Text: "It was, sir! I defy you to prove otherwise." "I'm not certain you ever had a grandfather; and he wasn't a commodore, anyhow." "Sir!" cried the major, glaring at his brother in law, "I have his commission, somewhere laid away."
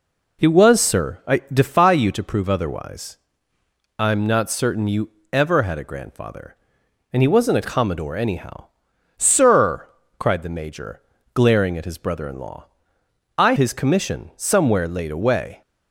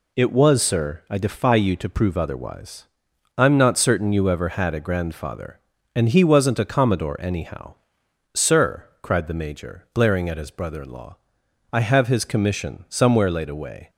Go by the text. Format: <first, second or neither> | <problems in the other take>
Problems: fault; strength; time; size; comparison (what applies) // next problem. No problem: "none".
second | pauses between "you" and "ever"; slight; at 5.0 s; 0.24 s long // skips "have"; at 13.5 s